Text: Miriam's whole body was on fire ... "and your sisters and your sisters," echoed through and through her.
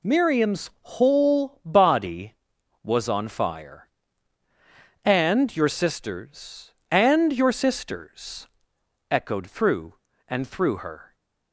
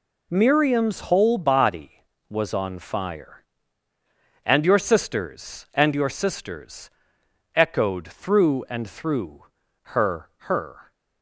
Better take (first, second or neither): first